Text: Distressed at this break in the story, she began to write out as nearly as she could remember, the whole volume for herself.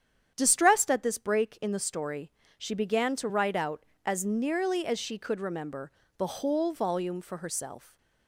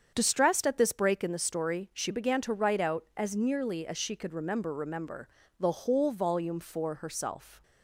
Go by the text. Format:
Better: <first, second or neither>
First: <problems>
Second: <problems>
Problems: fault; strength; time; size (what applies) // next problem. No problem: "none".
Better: first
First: starts louder than the rest; strong; until 1.3 s; 9 dB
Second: starts louder than the rest; strong; until 1.1 s; 7.5 dB // says "remember" twice; at 4.7 s